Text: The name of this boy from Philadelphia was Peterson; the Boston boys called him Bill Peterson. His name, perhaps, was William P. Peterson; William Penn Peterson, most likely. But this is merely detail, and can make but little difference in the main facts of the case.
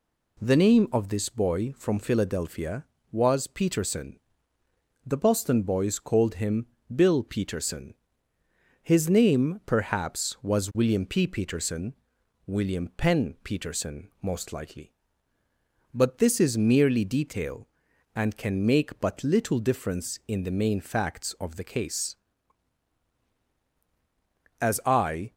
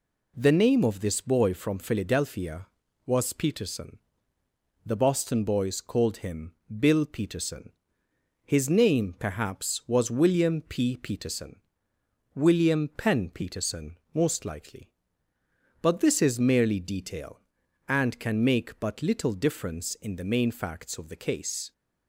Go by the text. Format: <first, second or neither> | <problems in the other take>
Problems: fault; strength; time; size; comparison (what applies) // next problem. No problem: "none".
second | pauses between "him" and "Bill"; slight; at 6.6 s; 0.28 s long; slight in the second // goes on to say "As I"; noticeable; from 24.5 s on; 0.74 s long